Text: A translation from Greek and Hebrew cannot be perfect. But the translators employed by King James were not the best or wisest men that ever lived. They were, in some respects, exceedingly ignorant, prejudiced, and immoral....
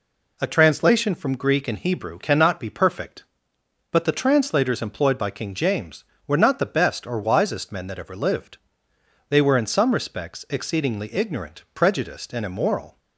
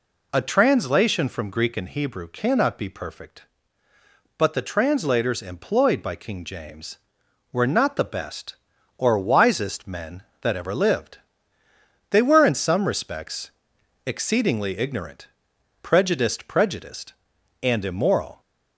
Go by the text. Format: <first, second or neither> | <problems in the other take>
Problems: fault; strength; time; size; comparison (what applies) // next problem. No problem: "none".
first | says "prejudiced" twice; at 16.4 s